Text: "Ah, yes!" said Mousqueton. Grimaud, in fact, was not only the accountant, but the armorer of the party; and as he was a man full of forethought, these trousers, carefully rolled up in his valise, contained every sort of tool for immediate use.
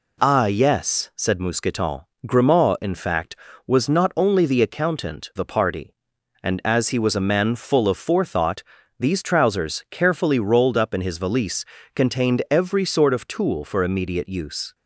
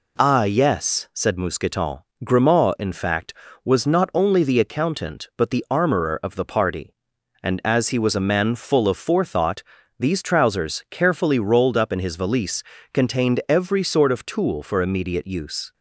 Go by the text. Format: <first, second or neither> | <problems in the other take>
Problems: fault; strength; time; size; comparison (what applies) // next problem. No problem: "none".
second | skips "but the armorer of"; at 5.3 s